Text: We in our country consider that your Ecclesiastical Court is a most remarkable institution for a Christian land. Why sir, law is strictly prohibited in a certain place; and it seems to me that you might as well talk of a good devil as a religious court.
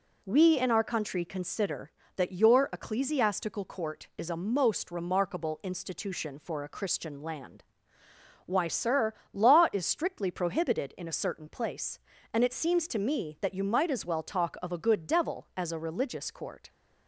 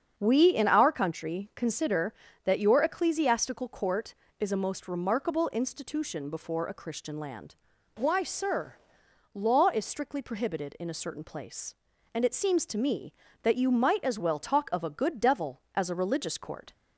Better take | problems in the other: first | starts louder than the rest; strong; until 1.1 s; 7 dB // says "before" for "for"; at 6.3 s

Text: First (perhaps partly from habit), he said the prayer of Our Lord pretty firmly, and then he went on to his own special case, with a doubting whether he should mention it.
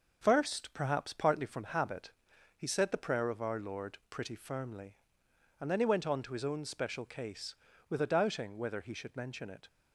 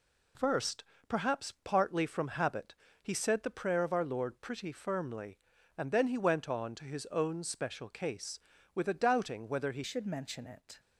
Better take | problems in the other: first | changes voice at "should"; from 9.8 s on; 0.9 s long

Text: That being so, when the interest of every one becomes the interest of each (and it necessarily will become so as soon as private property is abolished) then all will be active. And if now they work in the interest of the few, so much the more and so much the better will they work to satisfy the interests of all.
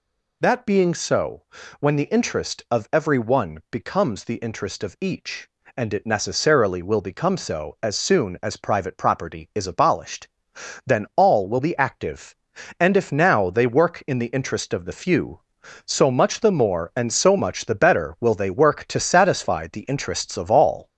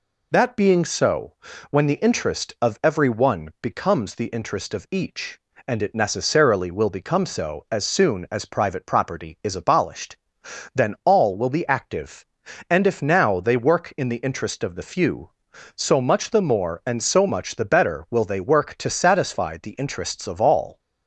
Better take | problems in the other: second | gets louder; throughout; 3.5 dB

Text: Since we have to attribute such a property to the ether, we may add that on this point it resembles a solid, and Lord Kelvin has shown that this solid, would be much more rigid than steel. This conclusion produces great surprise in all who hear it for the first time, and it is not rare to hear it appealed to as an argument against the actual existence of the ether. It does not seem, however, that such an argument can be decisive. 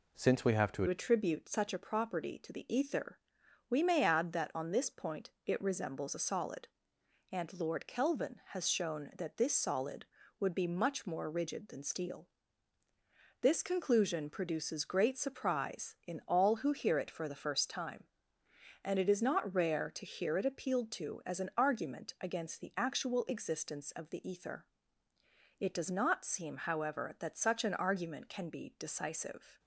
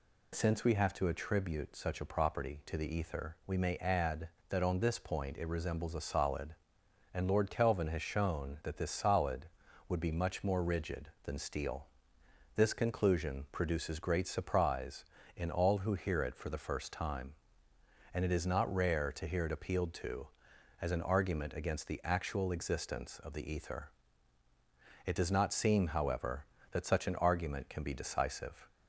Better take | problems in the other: second | changes voice at "attribute"; from 0.8 s on; 28.7 s long

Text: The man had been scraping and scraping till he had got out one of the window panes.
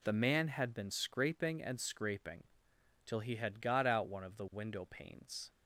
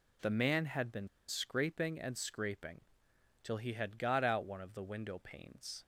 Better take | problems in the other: first | pauses between "been" and "scraping"; slight; at 1.0 s; 0.20 s long // pauses between "scraping" and "till"; noticeable; at 2.8 s; 0.58 s long; noticeable in the first

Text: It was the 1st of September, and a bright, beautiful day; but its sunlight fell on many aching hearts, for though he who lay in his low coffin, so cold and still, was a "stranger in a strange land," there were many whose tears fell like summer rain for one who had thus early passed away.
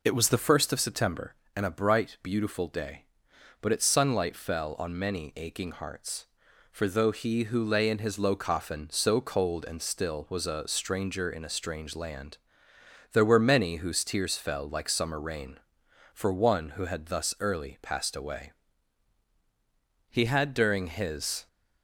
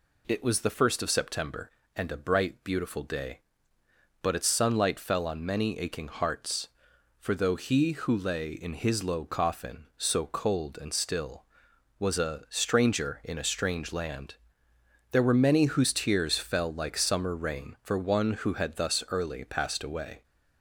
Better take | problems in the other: second | goes on to say "He had during his"; from 20.1 s on; 1.3 s long

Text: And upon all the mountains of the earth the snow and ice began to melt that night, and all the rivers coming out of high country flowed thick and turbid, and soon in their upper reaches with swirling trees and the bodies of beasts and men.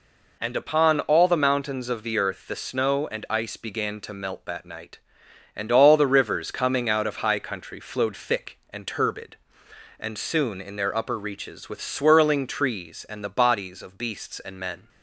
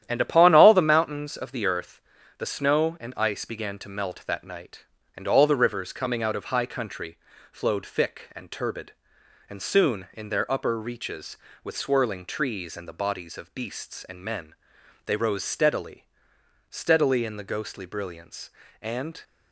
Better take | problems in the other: first | starts louder than the rest; strong; until 1.0 s; 11 dB // pauses between "earth" and "the"; slight; at 2.0 s; 0.36 s long // pauses between "country" and "flowed"; slight; at 7.1 s; 0.34 s long // goes on to say "They rose steadily steadily in the ghostly brilliance and"; strong; from 15.0 s on; 4.1 s long

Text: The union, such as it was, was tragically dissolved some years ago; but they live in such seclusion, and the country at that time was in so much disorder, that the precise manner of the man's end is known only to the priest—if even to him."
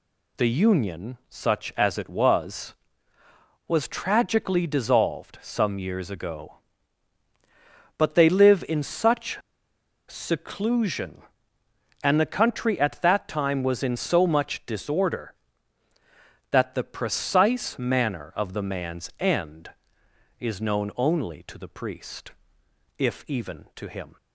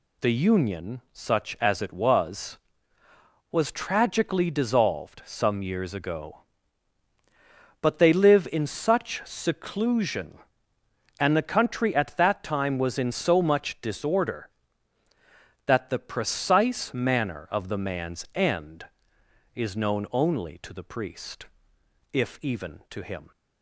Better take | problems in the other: second | pauses between "such" and "seclusion"; noticeable; at 9.3 s; 0.71 s long

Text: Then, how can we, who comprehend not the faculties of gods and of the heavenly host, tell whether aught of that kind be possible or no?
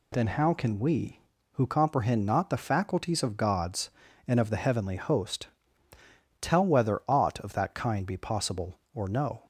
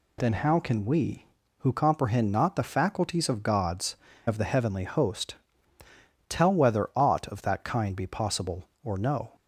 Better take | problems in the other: first | skips "and"; at 4.1 s

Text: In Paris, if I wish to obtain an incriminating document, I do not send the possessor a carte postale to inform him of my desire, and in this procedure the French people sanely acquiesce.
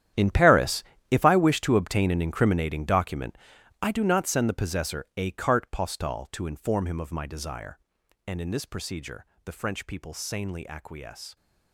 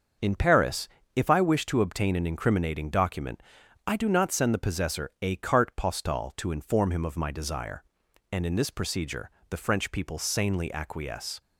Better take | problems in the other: second | gets quieter; strong; throughout; 16 dB // starts louder than the rest; strong; until 1.4 s; 10.5 dB; also in the second // pauses between "procedure" and "the"; slight; at 9.2 s; 0.20 s long; slight in the second

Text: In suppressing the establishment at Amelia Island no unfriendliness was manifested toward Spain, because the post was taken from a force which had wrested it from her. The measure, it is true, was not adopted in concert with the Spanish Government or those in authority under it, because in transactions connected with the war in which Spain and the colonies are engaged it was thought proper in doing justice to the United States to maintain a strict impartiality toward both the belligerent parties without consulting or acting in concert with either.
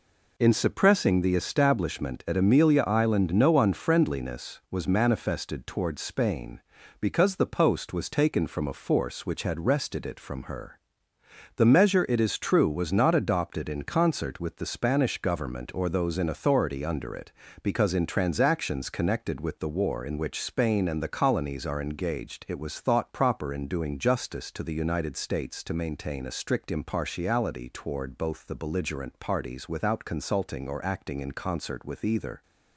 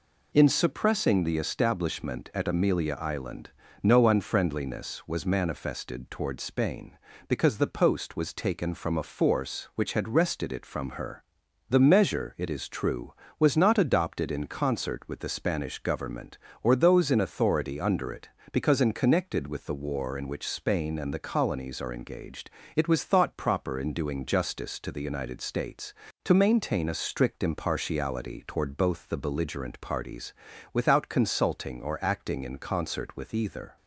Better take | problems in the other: first | pauses between "Island" and "no"; slight; at 3.4 s; 0.34 s long // skips "transactions"; at 18.9 s // pauses between "engaged" and "it"; slight; at 22.5 s; 0.24 s long // pauses between "parties" and "without"; at 30.3 s; 0.38 s long

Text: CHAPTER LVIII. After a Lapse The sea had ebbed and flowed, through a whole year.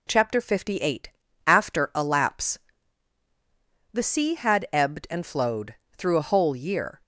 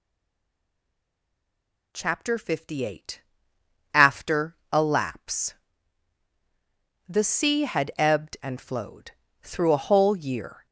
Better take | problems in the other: first | stays silent before the first word; noticeable; until 1.9 s; 1.9 s long // pauses between "After" and "a"; slight; at 4.5 s; 0.16 s long // pauses between "Lapse" and "The"; strong; at 5.5 s; 1.5 s long; strong in the first

